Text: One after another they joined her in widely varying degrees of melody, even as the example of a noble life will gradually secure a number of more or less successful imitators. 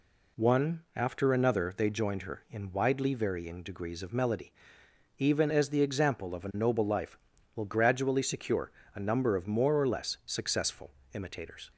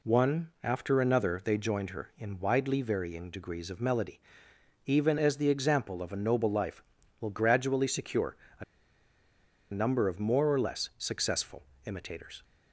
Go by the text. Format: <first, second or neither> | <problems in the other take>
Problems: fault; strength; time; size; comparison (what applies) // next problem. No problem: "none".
first | pauses between "secure" and "a"; slight; at 8.3 s; 0.22 s long; slight in the first // pauses between "a" and "number"; at 8.6 s; 1.0 s long // pauses between "successful" and "imitators"; slight; at 11.6 s; 0.22 s long; slight in the first